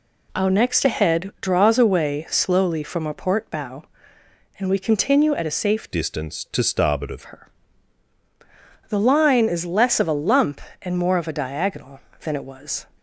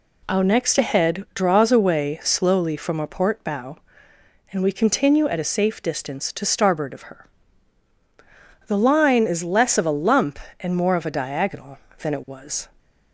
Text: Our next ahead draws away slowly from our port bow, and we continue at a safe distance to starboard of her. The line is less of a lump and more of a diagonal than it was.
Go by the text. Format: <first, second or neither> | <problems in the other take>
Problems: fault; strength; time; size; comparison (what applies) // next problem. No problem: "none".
second | changes voice from "distance" to "of"; from 5.9 to 7.2 s; 1.3 s long